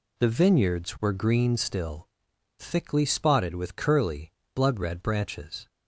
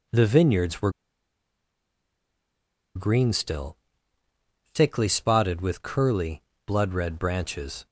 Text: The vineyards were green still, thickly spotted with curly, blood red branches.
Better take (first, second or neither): first